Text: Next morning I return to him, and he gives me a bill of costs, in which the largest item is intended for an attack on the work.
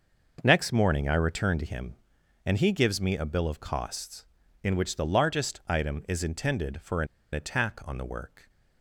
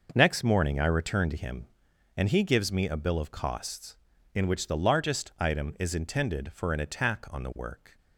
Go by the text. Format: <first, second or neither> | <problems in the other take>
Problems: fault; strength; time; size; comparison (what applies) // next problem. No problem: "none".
second | pauses between "an" and "attack"; slight; at 7.0 s; 0.28 s long